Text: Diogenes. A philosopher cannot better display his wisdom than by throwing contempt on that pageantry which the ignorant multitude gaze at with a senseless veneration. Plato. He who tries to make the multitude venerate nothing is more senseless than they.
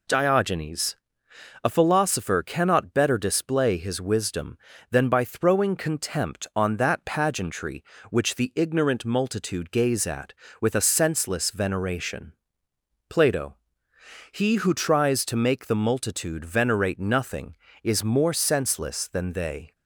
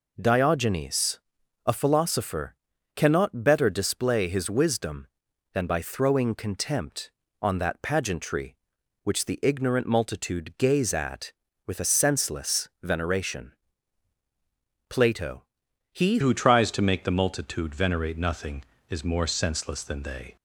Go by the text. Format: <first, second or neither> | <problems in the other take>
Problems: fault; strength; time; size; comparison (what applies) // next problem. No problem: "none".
first | pauses between "philosopher" and "cannot"; at 2.5 s; 0.40 s long // changes voice at "who"; from 16.2 s on; 4.1 s long